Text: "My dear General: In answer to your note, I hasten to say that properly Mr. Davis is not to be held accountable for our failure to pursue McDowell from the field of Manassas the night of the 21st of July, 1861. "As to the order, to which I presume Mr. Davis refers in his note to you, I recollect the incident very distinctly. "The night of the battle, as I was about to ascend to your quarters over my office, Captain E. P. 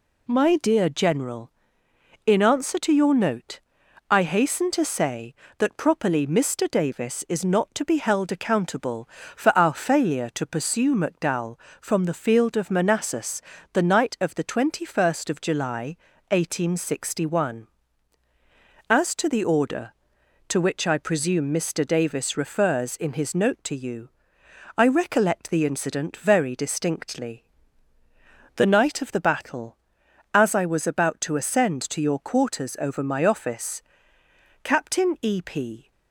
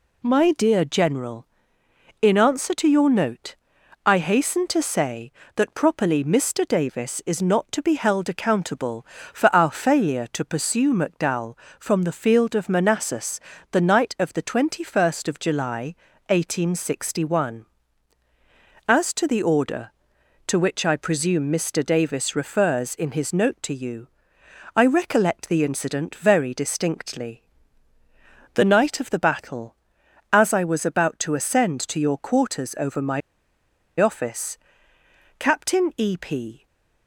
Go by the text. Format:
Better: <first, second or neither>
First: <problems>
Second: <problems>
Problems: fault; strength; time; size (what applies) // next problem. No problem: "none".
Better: first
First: pauses between "Manassas" and "the"; slight; at 13.4 s; 0.32 s long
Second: pauses between "Manassas" and "the"; slight; at 13.4 s; 0.32 s long // pauses between "my" and "office"; noticeable; at 33.2 s; 0.79 s long // stays silent after the last word; slight; from 36.5 s on; 0.5 s long